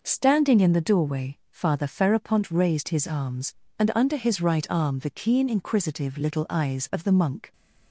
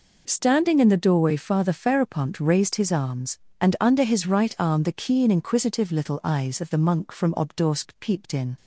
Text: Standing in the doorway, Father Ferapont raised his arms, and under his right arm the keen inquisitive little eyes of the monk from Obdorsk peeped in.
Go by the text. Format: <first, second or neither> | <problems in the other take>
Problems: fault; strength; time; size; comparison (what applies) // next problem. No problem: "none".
second | stops before "from Obdorsk peeped in"; at 7.5 s